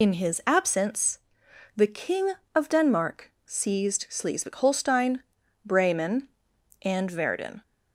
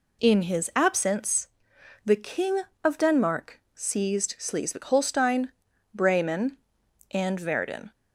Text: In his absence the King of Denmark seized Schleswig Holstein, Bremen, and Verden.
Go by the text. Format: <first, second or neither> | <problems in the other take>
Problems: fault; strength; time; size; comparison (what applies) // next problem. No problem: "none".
second | loses the start of "In"; at 0.0 s; 90 ms // pauses between "absence" and "the"; noticeable; at 1.1 s; 0.58 s long; noticeable in the second